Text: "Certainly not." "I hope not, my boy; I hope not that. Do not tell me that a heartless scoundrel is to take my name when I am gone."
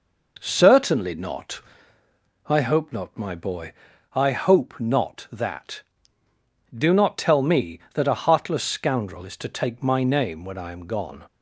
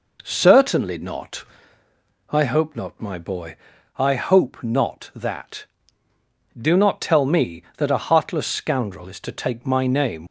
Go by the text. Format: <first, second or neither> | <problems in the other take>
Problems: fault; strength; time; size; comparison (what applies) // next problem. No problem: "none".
first | stops before "when I am gone"; at 10.2 s